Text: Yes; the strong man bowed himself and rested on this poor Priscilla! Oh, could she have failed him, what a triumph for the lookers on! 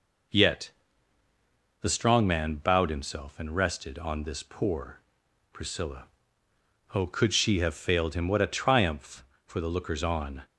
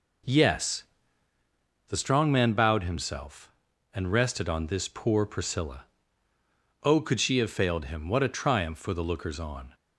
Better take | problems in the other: second | says "Yet" for "Yes"; at 0.3 s // pauses between "poor" and "Priscilla"; noticeable; at 5.0 s; 0.52 s long

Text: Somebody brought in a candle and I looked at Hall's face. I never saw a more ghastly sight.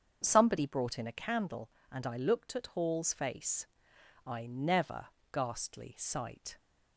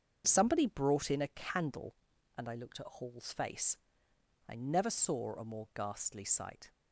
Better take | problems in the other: second | starts louder than the rest; until 1.2 s; 7 dB; strong in the second // skips "saw a more"; at 5.1 s

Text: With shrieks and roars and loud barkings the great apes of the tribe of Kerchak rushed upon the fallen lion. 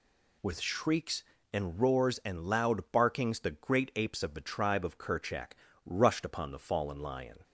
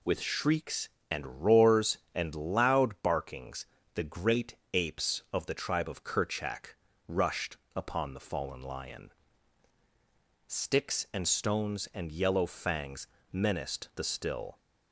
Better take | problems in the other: first | pauses between "barkings" and "the"; slight; at 3.6 s; 0.28 s long // pauses between "great" and "apes"; slight; at 4.5 s; 0.18 s long // pauses between "Kerchak" and "rushed"; slight; at 6.7 s; 0.30 s long; slight in the first // pauses between "rushed" and "upon"; slight; at 7.5 s; 0.20 s long // goes on to say "Sticks and stones and yellow fangs menaced the still"; strong; from 10.4 s on; 4.1 s long

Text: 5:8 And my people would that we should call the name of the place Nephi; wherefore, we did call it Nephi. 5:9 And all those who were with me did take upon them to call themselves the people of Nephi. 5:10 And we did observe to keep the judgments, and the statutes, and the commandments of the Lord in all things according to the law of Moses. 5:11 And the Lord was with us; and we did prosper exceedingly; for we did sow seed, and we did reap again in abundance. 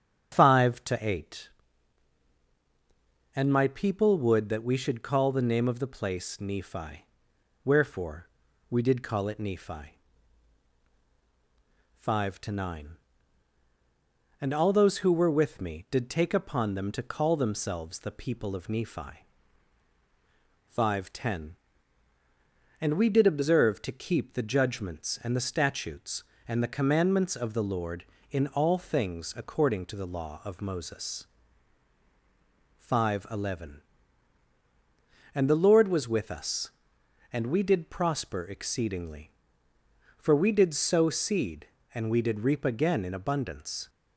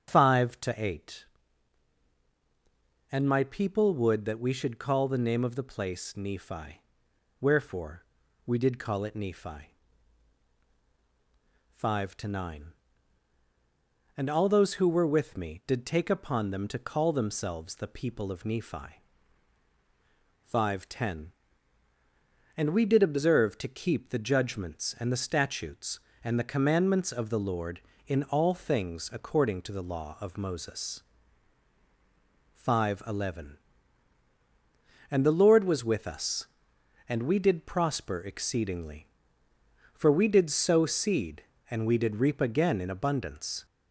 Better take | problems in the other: first | gets louder; slight; throughout; 2.5 dB // starts louder than the rest; strong; until 1.1 s; 8.5 dB; strong in the first

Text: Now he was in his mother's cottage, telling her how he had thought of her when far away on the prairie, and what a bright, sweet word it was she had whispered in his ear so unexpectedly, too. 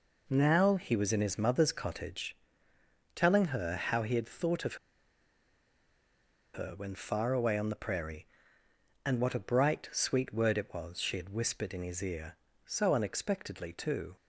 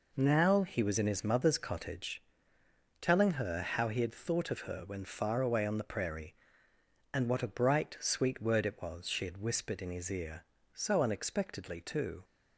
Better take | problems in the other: second | pauses between "of" and "her"; strong; at 4.7 s; 1.7 s long

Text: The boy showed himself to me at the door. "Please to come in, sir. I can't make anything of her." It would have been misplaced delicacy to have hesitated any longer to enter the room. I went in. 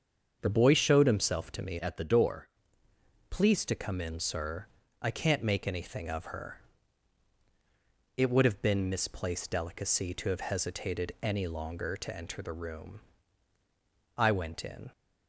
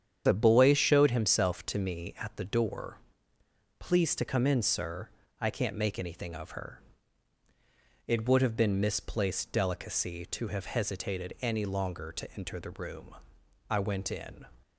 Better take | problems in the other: second | starts louder than the rest; until 1.4 s; 7 dB; strong in the second // changes voice from "at" to "door"; from 1.7 to 2.4 s; 0.7 s long

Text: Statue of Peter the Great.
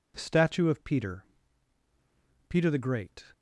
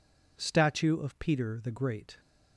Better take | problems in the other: second | says "Peter" twice; at 2.4 s

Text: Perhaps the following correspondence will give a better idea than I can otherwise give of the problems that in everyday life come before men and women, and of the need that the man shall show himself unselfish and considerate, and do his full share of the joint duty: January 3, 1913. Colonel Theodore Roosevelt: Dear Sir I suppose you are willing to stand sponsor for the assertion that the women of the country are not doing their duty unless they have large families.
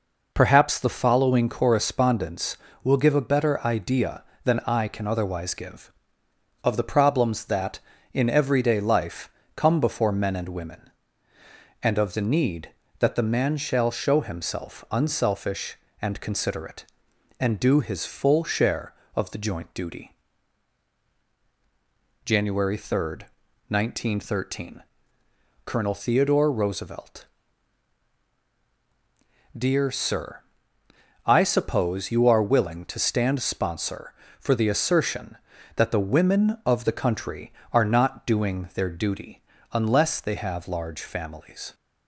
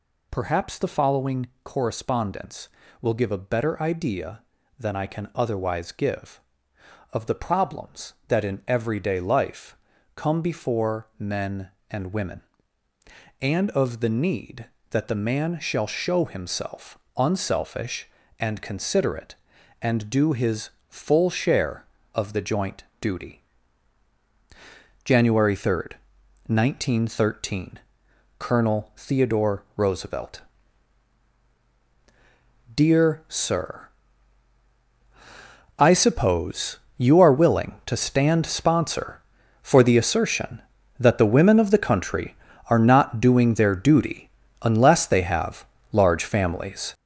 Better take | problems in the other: first | gets louder; strong; throughout; 7.5 dB // pauses between "following" and "correspondence"; slight; at 1.4 s; 0.16 s long // pauses between "life" and "come"; at 9.7 s; 0.38 s long; slight in the first // pauses between "himself" and "unselfish"; slight; at 16.9 s; 0.18 s long // pauses between "his" and "full"; slight; at 20.6 s; 0.18 s long // pauses between "joint" and "duty"; slight; at 22.8 s; 0.18 s long // pauses between "Sir" and "I"; strong; at 33.8 s; 1.8 s long; noticeable in the first // pauses between "suppose" and "you"; slight; at 36.7 s; 0.20 s long // pauses between "duty" and "unless"; slight; at 44.2 s; 0.32 s long; slight in the first // pauses between "have" and "large"; slight; at 45.6 s; 0.26 s long

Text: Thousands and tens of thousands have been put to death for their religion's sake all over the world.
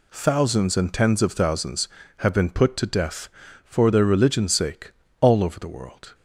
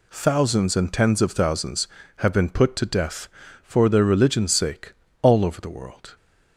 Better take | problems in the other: neither | pauses between "sake" and "all"; slight; the same in both

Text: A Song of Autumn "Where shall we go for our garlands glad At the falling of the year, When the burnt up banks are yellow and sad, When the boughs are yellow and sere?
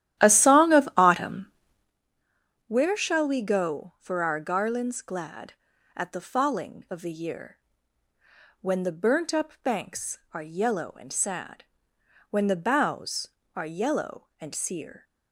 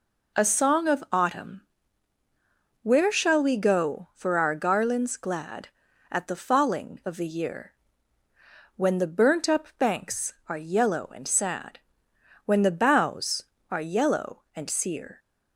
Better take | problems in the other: second | starts louder than the rest; strong; until 2.0 s; 12.5 dB // pauses between "Autumn" and "Where"; at 1.4 s; 1.2 s long; also in the second

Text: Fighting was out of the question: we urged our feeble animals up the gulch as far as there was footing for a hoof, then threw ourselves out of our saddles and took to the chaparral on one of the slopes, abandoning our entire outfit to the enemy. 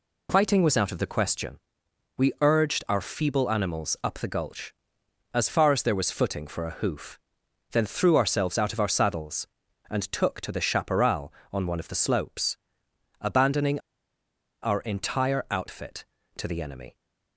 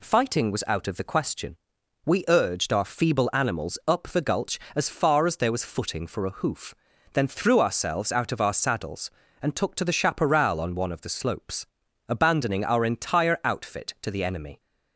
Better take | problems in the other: second | pauses between "abandoning" and "our"; noticeable; at 13.8 s; 0.81 s long

